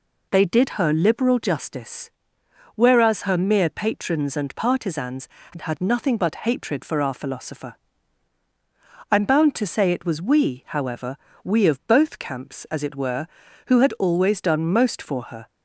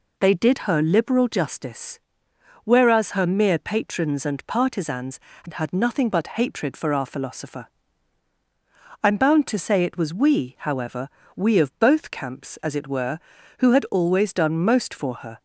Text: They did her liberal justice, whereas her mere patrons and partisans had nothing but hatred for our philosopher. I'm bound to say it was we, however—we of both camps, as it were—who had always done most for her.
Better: neither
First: none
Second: none

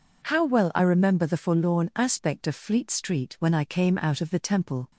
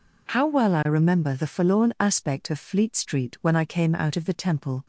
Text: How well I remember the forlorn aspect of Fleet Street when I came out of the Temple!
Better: neither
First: none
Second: none

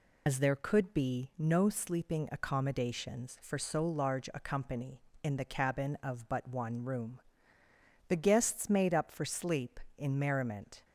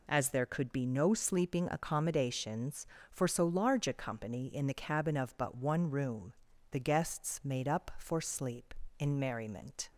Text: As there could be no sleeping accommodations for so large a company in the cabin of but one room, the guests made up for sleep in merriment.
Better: second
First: loses the start of "As"; at 0.2 s; 55 ms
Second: none

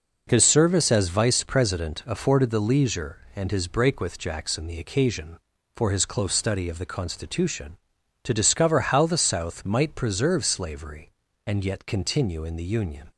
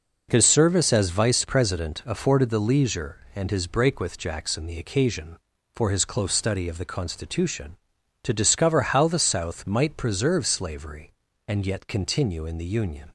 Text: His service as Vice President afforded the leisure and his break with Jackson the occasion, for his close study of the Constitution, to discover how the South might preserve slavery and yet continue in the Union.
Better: neither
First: none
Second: none

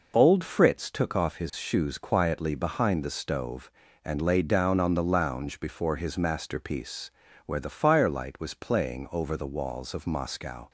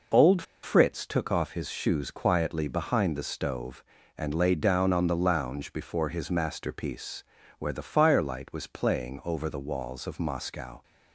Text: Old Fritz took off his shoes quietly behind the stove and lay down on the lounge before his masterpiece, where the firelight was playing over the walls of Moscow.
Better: first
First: none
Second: pauses between "Old" and "Fritz"; slight; at 0.4 s; 0.20 s long

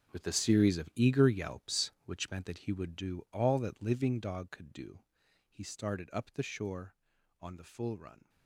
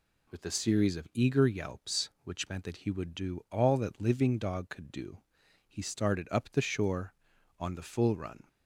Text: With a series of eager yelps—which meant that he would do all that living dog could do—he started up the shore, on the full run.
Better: second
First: gets quieter; strong; throughout; 14.5 dB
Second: none

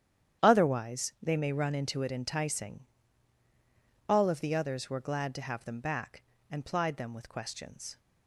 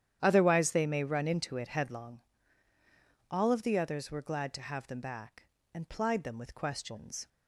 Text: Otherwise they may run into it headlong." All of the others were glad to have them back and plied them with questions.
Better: second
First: starts louder than the rest; strong; until 1.5 s; 10 dB // says "enticing" for "headlong"; at 2.1 s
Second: starts louder than the rest; strong; until 1.2 s; 10 dB

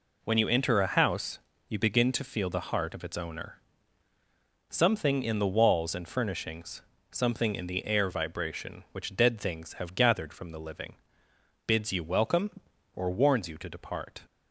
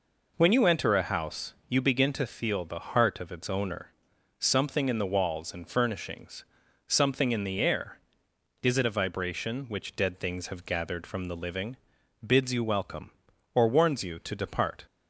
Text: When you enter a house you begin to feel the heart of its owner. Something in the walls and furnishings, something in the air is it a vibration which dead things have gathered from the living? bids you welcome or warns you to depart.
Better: second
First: pauses between "house" and "you"; slight; at 1.3 s; 0.28 s long // skips "is it a"; at 8.0 s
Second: none

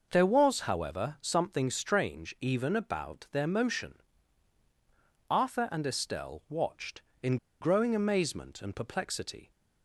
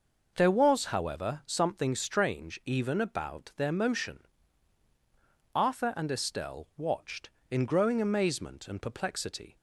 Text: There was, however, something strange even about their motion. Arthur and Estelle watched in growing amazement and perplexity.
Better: second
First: pauses between "in" and "growing"; slight; at 7.3 s; 0.24 s long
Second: none

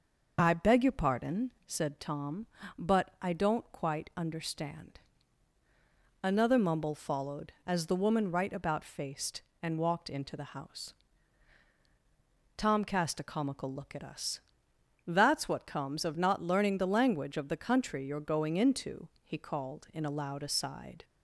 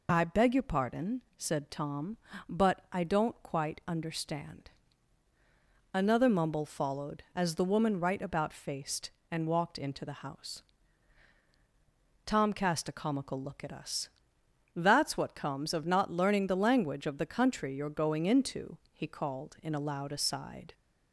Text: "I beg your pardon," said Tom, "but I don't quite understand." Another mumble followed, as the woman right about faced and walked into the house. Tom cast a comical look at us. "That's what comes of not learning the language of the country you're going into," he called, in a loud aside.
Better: second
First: starts louder than the rest; noticeable; until 1.7 s; 6 dB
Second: none

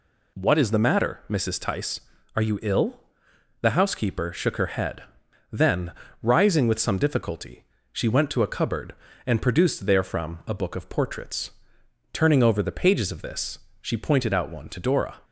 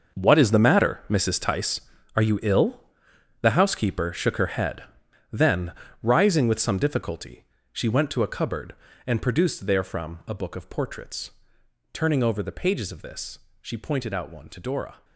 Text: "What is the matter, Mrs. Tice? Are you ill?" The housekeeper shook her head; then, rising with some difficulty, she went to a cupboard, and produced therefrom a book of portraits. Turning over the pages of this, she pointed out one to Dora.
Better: first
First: none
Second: gets quieter; strong; throughout; 13 dB

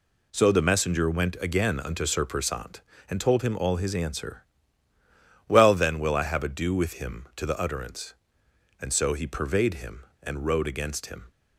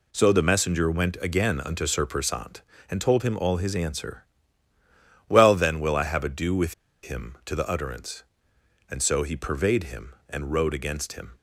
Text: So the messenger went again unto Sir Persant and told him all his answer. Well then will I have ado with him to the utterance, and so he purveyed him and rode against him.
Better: first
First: none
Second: pauses between "with" and "him"; slight; at 6.7 s; 0.28 s long

